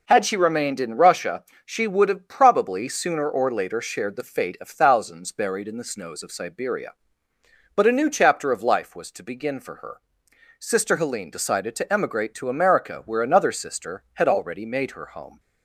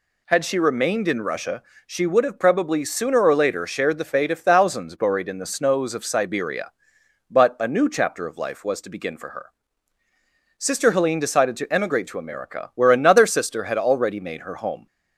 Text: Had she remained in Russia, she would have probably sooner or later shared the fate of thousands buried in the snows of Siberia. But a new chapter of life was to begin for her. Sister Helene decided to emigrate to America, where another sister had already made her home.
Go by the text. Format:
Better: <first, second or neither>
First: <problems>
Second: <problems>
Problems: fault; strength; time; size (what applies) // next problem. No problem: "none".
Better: neither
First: none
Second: none